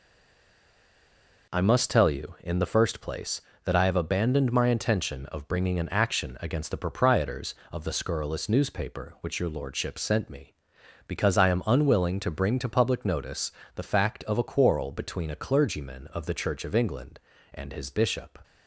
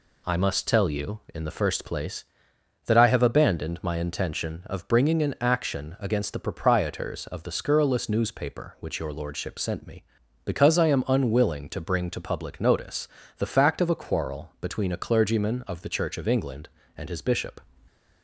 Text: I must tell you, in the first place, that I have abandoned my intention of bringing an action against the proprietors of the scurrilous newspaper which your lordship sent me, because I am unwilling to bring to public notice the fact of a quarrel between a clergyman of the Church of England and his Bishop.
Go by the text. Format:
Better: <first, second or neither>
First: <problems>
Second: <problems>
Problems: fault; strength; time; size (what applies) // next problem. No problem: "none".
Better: second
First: stays silent before the first word; noticeable; until 1.4 s; 1.4 s long // pauses between "notice" and "the"; slight; at 13.4 s; 0.26 s long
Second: pauses between "notice" and "the"; slight; at 13.0 s; 0.32 s long